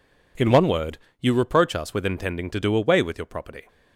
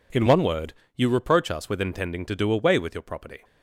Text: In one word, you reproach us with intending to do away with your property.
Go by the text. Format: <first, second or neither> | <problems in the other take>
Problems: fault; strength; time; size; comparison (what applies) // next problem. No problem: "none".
neither | none